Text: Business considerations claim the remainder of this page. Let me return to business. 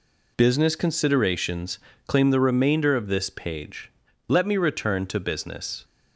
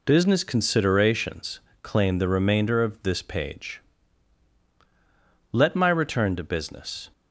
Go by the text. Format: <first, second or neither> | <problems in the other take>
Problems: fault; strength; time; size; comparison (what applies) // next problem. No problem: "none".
first | pauses between "considerations" and "claim"; slight; at 1.5 s; 0.24 s long; slight in the first // says "my" for "me"; at 5.7 s